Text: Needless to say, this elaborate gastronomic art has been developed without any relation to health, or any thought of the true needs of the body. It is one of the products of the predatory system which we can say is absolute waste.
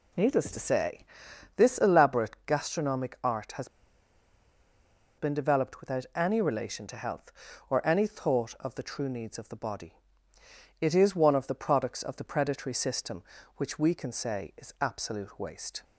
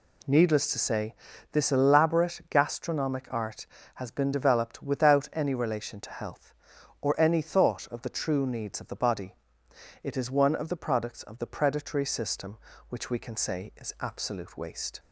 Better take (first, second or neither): second